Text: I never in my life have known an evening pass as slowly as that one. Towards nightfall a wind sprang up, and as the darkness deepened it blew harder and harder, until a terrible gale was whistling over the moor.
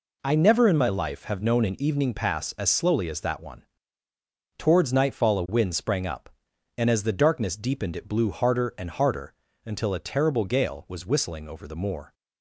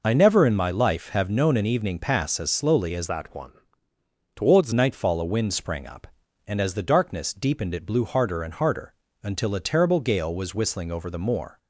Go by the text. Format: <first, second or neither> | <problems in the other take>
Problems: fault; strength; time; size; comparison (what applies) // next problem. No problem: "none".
first | changes voice from "that" to "Towards"; from 3.0 to 4.7 s; 1.7 s long